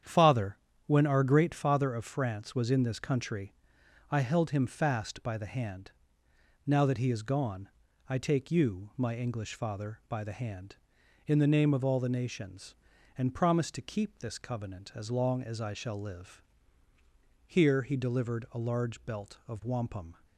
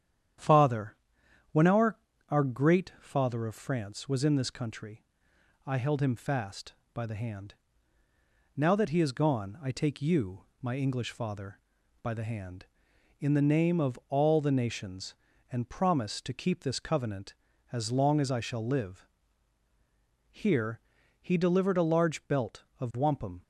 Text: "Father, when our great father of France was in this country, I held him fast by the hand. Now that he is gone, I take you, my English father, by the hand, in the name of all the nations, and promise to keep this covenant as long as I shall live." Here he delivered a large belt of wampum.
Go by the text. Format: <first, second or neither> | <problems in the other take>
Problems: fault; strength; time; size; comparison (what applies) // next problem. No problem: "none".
first | starts louder than the rest; strong; until 1.9 s; 9.5 dB; strong in the first // says "our" twice; at 2.2 s // pauses between "Here" and "he"; at 20.7 s; 0.42 s long